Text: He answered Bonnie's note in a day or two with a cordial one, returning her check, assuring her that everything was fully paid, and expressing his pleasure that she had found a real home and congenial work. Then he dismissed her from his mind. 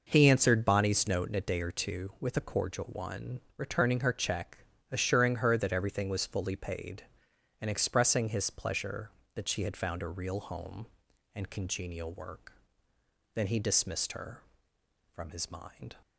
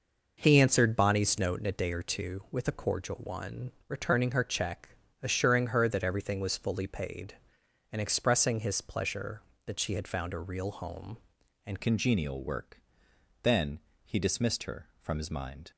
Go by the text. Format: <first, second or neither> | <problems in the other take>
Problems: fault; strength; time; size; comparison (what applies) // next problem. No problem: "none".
first | changes voice at "congenial"; from 11.8 s on; 3.9 s long // pauses between "Then" and "he"; slight; at 13.7 s; 0.26 s long